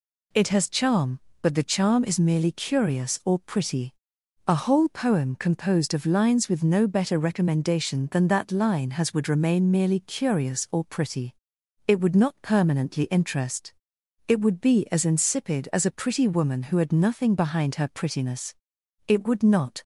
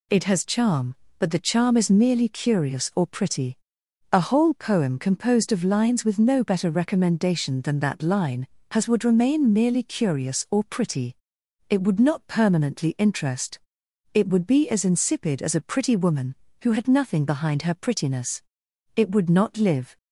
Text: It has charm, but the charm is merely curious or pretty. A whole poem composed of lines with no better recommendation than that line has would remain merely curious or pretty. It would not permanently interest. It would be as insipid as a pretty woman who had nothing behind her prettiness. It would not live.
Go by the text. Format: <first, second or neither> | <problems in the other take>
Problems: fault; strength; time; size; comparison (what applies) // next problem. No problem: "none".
second | stops before "live"; at 19.8 s